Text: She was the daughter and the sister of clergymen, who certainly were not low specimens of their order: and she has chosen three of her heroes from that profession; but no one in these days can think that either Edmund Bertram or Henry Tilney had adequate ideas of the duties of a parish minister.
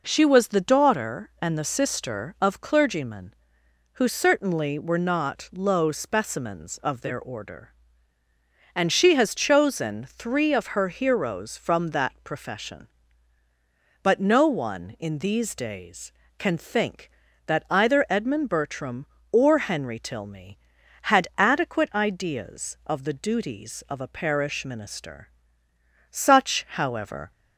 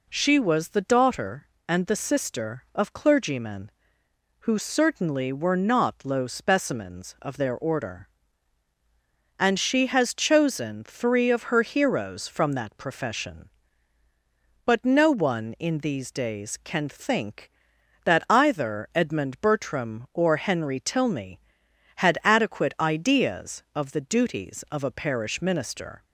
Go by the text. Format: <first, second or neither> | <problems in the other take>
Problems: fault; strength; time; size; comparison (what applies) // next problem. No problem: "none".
second | goes on to say "Such however"; noticeable; from 26.1 s on; 1.2 s long